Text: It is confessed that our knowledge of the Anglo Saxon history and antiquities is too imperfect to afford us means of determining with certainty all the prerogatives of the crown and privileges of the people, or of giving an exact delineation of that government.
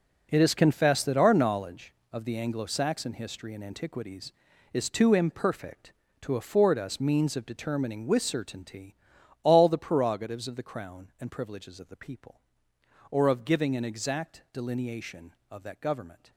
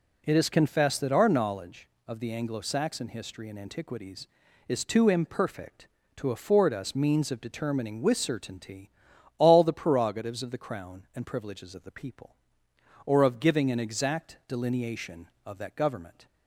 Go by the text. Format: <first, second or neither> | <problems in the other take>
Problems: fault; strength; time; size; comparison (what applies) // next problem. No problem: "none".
second | gets quieter; strong; throughout; 12.5 dB // pauses between "certainty" and "all"; noticeable; at 8.9 s; 0.48 s long; noticeable in the second